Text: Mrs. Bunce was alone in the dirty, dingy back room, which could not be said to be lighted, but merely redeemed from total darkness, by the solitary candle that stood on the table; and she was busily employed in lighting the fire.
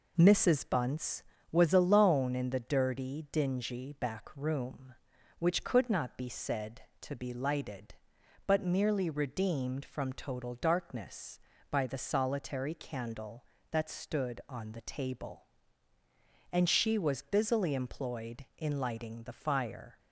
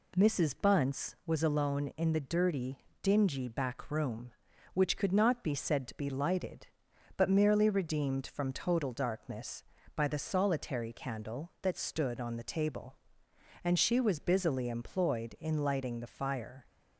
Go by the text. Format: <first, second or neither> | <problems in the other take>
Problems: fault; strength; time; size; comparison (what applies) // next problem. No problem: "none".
neither | none